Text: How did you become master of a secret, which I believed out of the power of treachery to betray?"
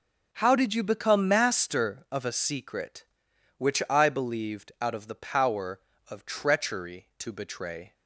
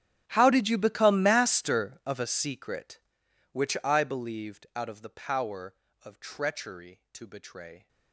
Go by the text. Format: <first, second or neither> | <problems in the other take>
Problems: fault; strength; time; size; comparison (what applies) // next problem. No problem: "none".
first | gets quieter; strong; throughout; 22 dB